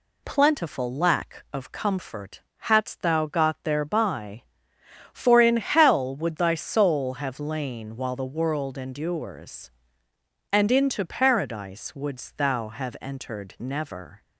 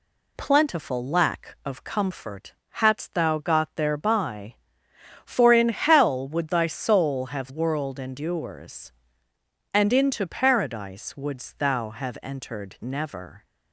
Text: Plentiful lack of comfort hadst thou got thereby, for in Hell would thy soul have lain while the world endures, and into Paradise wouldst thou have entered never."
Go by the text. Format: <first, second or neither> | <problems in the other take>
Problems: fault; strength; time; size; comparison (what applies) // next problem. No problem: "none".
first | pauses between "comfort" and "hadst"; slight; at 2.5 s; 0.18 s long; slight in the first // skips "lain while the"; at 7.4 s